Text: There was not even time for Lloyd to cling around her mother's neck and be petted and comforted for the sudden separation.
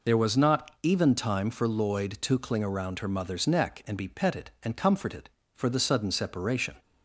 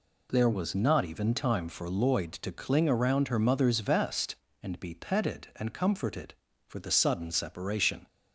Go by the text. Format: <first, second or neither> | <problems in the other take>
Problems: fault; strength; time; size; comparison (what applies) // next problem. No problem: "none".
first | says "vest" for "neck"; at 3.8 s